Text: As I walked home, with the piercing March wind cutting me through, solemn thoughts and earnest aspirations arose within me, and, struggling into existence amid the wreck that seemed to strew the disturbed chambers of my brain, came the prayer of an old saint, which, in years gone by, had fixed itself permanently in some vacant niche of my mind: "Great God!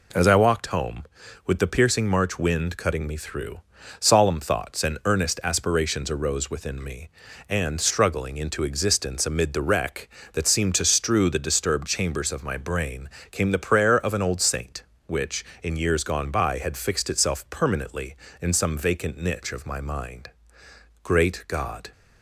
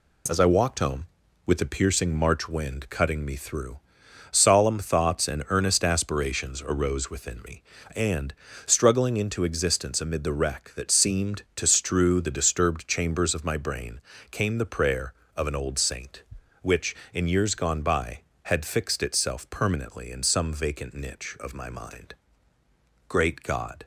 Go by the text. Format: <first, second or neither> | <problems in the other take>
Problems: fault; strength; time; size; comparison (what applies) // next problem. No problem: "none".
neither | none